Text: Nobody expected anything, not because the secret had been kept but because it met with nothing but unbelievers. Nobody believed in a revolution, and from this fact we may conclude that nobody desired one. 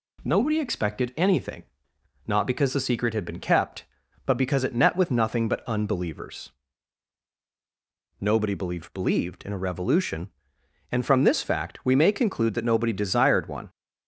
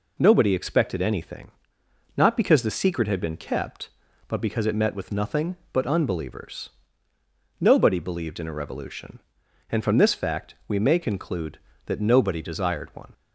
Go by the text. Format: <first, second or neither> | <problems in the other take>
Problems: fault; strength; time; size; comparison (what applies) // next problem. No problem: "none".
second | says "believed" twice; at 8.9 s